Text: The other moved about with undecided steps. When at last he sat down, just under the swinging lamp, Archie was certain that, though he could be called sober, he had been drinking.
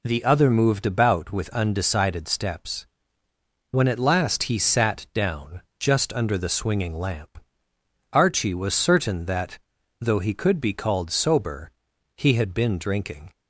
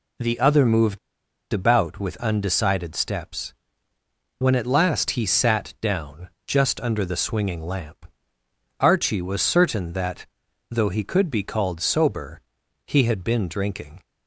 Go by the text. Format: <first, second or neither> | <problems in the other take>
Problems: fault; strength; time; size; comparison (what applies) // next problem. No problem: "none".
first | pauses between "moved" and "about"; noticeable; at 0.9 s; 0.53 s long